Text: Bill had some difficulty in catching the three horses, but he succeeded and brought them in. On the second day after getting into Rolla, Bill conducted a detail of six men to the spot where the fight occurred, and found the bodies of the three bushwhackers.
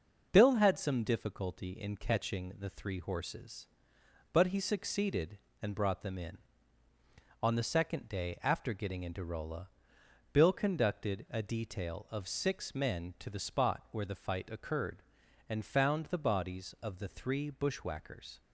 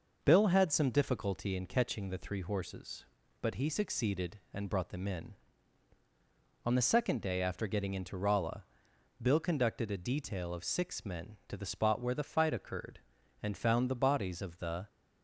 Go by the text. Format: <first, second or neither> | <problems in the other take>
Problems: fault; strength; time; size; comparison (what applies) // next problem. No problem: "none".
first | stops before "three bushwhackers"; at 14.8 s